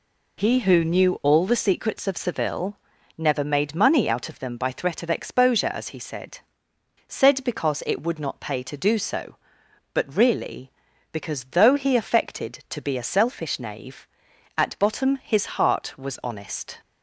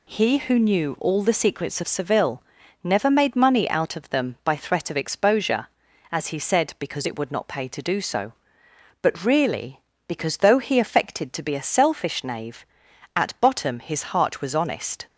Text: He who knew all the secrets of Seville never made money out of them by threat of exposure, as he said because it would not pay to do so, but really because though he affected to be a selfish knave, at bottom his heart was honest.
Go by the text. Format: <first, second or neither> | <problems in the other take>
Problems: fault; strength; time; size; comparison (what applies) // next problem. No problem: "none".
second | pauses between "Seville" and "never"; at 2.7 s; 0.40 s long; also in the second // says "said" twice; at 7.0 s